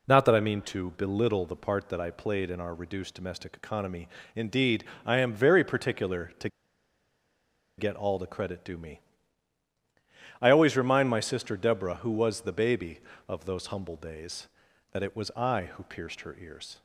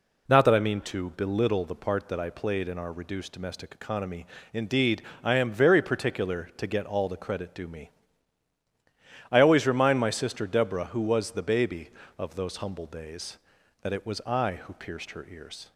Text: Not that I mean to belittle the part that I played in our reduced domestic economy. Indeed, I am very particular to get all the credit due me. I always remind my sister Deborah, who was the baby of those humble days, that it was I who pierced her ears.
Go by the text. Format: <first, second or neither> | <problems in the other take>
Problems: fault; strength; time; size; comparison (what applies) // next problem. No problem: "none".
second | pauses between "to" and "get"; strong; at 6.4 s; 1.2 s long